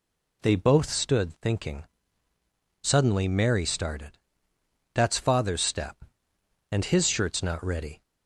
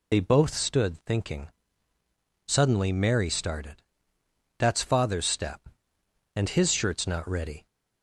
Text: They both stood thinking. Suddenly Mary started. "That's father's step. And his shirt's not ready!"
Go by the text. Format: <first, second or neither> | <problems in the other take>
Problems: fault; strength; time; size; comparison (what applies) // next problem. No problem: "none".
first | loses the start of "They"; at 0.1 s; 60 ms